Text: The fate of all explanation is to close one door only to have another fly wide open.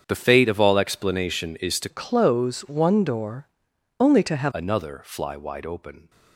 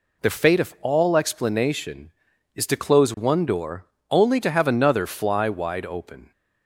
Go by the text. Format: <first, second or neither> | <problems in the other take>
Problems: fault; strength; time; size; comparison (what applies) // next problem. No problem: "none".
second | starts louder than the rest; strong; until 1.0 s; 7.5 dB // changes voice from "close" to "have"; from 1.8 to 4.5 s; 2.7 s long // pauses between "door" and "only"; noticeable; at 3.4 s; 0.54 s long; slight in the second